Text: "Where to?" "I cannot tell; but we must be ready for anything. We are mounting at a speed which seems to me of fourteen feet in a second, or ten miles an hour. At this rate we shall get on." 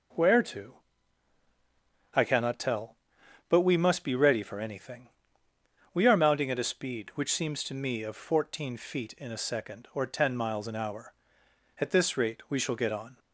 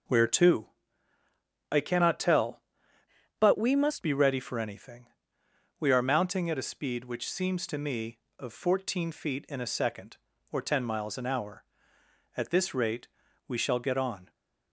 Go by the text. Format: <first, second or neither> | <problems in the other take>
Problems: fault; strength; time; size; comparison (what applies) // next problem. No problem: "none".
first | changes voice from "but" to "must"; from 3.3 to 4.0 s; 0.7 s long // pauses between "rate" and "we"; at 13.0 s; 0.40 s long